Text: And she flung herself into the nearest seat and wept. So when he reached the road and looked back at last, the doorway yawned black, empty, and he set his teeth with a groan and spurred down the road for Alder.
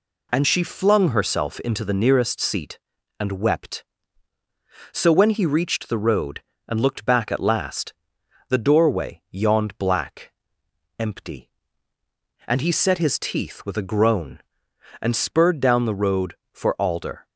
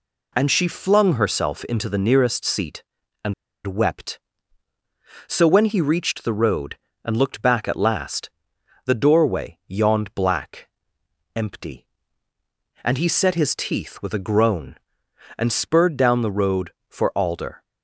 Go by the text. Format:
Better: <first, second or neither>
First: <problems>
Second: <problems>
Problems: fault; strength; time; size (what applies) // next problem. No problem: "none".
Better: first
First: none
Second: pauses between "and" and "wept"; slight; at 3.3 s; 0.33 s long